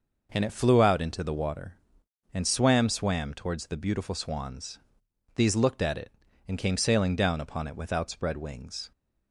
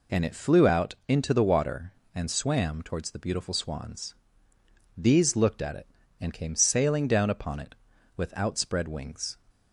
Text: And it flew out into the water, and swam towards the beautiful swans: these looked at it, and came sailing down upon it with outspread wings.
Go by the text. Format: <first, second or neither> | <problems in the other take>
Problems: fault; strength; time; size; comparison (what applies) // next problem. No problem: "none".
second | says "swam" twice; at 2.8 s